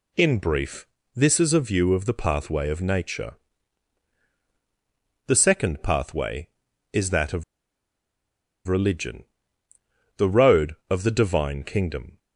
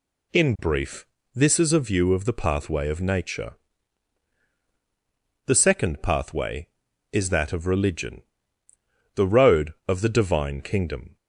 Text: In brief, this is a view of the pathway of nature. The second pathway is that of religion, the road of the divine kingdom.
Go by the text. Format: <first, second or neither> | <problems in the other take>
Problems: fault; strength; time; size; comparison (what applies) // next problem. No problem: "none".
second | pauses between "of" and "religion"; at 7.4 s; 1.2 s long